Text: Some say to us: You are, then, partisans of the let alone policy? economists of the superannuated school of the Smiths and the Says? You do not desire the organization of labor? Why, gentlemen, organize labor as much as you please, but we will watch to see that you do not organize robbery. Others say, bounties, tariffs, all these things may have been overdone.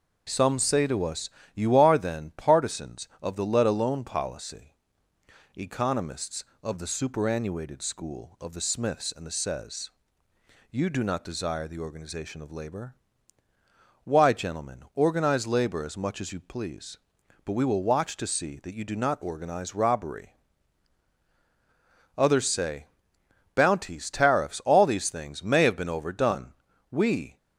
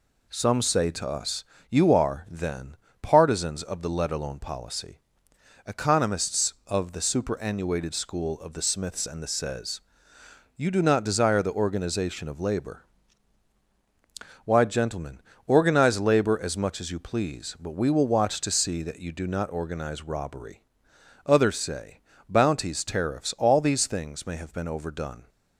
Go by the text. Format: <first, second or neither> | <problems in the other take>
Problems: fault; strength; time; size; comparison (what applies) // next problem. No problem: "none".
second | goes on to say "We"; slight; from 26.9 s on; 0.46 s long